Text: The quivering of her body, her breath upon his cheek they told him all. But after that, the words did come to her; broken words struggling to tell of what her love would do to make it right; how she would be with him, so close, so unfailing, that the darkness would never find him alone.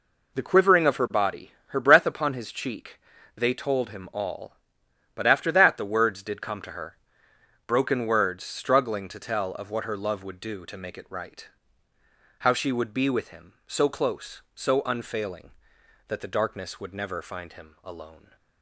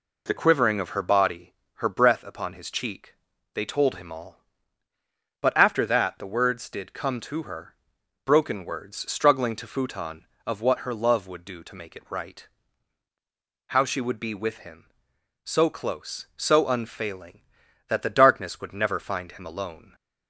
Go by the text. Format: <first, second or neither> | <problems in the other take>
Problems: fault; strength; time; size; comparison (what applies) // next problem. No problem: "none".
first | pauses between "cheek" and "they"; at 3.1 s; 0.40 s long; also in the first // says "futon" for "tell"; at 9.6 s